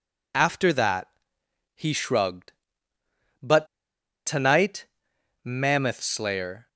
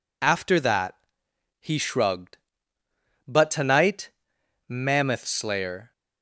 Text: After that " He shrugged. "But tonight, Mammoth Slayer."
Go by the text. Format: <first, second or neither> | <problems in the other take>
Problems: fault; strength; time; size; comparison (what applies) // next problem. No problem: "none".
second | pauses between "But" and "tonight"; noticeable; at 3.6 s; 0.60 s long